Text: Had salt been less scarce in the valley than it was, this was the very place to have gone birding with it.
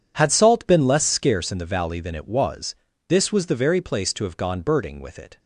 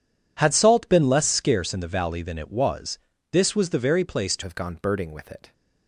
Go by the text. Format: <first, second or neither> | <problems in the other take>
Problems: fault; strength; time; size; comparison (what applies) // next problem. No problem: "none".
first | changes voice at "have"; from 4.4 s on; 1.1 s long